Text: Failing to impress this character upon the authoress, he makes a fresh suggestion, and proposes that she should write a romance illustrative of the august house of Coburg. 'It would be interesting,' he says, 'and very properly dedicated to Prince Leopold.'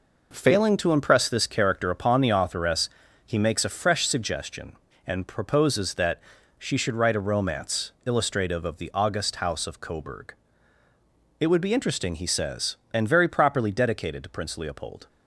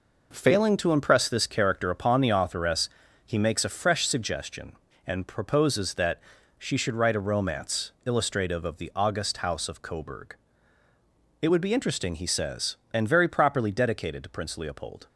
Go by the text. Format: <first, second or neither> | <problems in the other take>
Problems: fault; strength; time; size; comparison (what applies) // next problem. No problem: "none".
neither | pauses between "that" and "she"; slight; the same in both